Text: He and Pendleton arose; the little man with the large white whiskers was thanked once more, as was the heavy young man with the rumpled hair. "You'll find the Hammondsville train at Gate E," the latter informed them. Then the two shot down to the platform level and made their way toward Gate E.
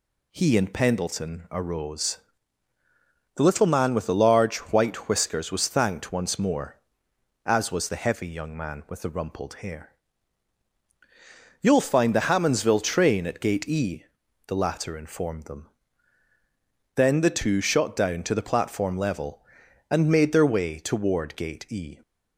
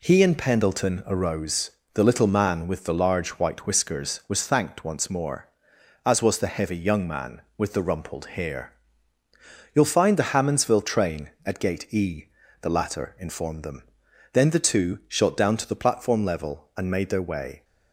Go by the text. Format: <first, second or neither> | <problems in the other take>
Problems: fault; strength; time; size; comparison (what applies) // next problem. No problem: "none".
first | stops before "toward Gate E"; at 17.6 s